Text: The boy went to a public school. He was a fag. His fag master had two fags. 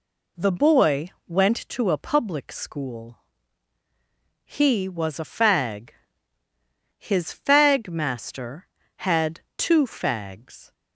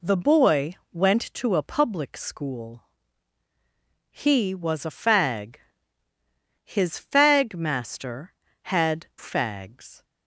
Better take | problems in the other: first | pauses between "boy" and "went"; slight; at 0.7 s; 0.18 s long; slight in the first // skips "two"; at 9.1 s

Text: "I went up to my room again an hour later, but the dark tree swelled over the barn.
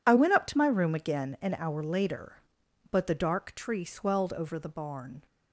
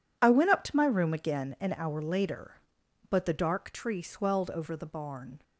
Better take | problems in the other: neither | none

